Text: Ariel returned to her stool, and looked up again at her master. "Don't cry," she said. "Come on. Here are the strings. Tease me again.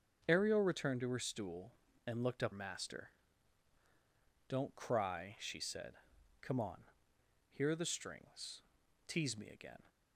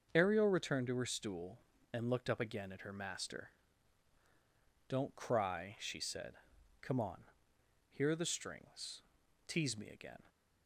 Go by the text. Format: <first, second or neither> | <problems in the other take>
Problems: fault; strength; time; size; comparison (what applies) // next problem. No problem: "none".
second | starts louder than the rest; strong; until 1.2 s; 7 dB; also in the second // skips "again at her"; at 2.5 s